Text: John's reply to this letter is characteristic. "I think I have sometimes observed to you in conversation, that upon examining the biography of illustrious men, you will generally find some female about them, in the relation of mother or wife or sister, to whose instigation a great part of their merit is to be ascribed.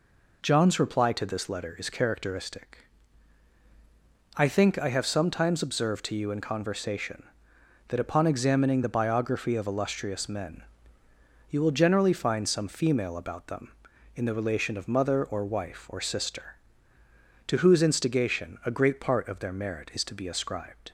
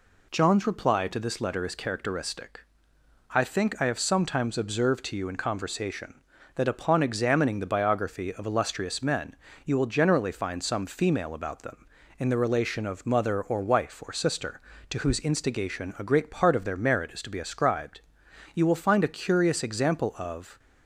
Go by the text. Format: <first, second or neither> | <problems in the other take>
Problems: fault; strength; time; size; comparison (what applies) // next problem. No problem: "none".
first | goes on to say "You will find a curious example of"; strong; from 18.5 s on; 2.0 s long